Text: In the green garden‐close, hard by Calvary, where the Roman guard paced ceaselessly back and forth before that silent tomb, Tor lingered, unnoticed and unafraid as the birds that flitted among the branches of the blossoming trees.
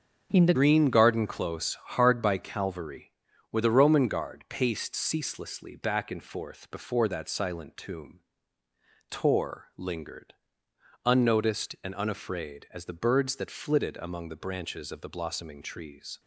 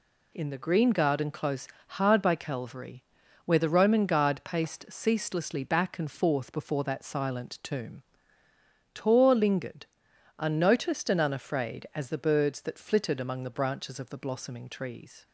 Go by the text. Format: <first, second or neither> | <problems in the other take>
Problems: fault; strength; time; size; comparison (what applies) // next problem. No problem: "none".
second | starts louder than the rest; until 1.3 s; 6.5 dB // changes voice at "green"; from 0.5 s on; 15.6 s long